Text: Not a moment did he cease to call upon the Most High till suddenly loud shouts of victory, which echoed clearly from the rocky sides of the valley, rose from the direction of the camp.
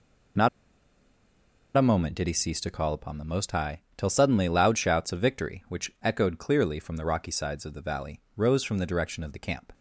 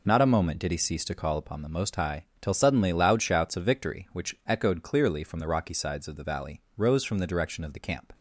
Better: second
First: pauses between "Not" and "a"; strong; at 0.4 s; 1.2 s long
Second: none

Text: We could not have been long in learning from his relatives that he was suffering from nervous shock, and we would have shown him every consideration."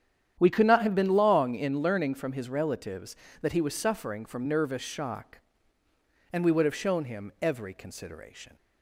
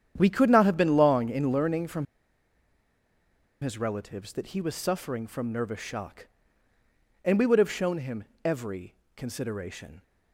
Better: first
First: starts louder than the rest; strong; until 1.3 s; 9.5 dB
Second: starts louder than the rest; strong; until 1.1 s; 9 dB // pauses between "from" and "his"; strong; at 2.0 s; 1.5 s long // pauses between "him" and "every"; slight; at 8.2 s; 0.20 s long // pauses between "every" and "consideration"; slight; at 8.9 s; 0.24 s long

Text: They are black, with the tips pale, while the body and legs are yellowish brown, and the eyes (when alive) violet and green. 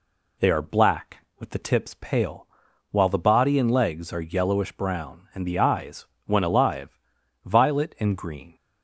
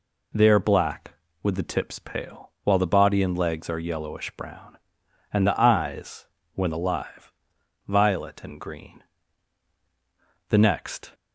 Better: first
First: none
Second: goes on to say "The next"; noticeable; from 10.4 s on; 0.62 s long

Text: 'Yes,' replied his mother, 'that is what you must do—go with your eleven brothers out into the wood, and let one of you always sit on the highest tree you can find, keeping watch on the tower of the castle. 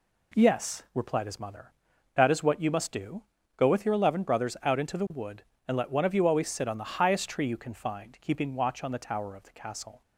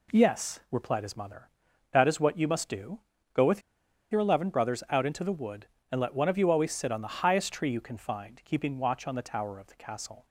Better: first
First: none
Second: pauses between "with" and "your"; noticeable; at 3.6 s; 0.49 s long

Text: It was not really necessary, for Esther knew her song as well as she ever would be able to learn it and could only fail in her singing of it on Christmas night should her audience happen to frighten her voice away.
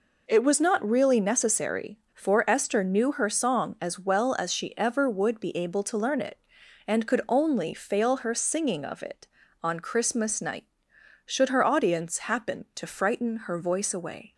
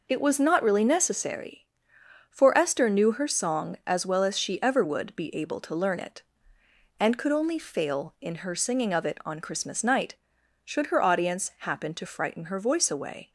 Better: second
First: skips "in"; at 8.1 s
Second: none

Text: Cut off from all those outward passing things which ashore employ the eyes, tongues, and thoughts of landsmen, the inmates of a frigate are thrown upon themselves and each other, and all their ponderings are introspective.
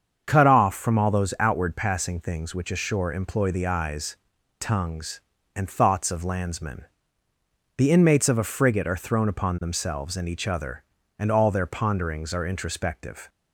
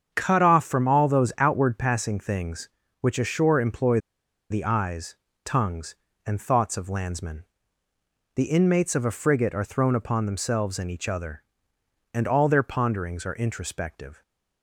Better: first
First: starts louder than the rest; until 1.2 s; 7 dB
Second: starts louder than the rest; strong; until 1.1 s; 7.5 dB // pauses between "employ" and "the"; noticeable; at 3.9 s; 0.52 s long

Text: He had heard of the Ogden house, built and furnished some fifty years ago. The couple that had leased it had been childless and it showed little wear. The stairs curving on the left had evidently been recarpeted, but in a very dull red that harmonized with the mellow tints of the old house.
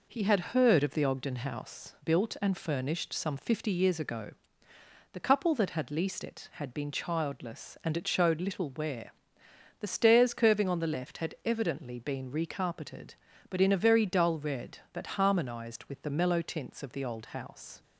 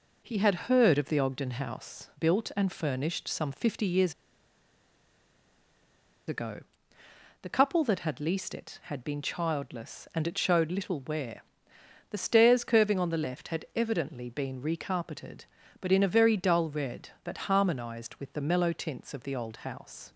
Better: first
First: none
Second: pauses between "years" and "ago"; strong; at 4.1 s; 2.1 s long

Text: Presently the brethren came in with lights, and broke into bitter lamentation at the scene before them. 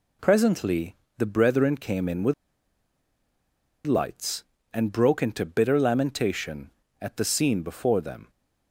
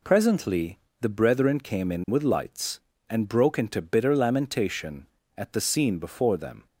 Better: second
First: pauses between "Presently" and "the"; slight; at 0.9 s; 0.22 s long // pauses between "with" and "lights"; strong; at 2.3 s; 1.5 s long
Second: pauses between "Presently" and "the"; slight; at 0.7 s; 0.22 s long

